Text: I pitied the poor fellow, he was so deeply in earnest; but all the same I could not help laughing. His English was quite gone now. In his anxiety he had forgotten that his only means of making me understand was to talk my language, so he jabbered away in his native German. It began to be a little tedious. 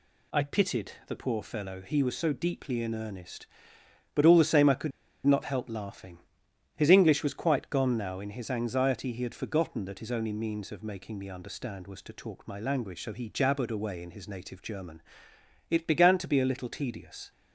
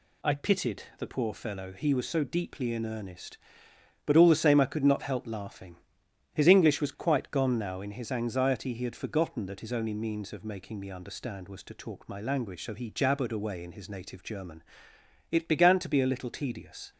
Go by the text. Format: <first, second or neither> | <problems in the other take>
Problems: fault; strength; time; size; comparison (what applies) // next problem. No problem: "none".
second | pauses between "could" and "not"; slight; at 4.9 s; 0.35 s long